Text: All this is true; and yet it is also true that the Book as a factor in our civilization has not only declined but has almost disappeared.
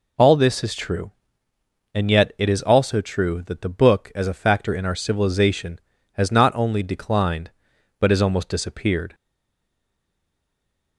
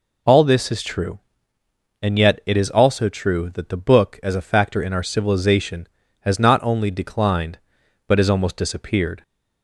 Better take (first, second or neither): second